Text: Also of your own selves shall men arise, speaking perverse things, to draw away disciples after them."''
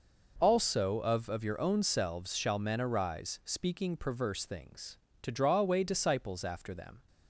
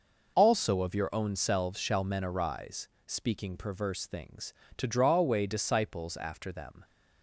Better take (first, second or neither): second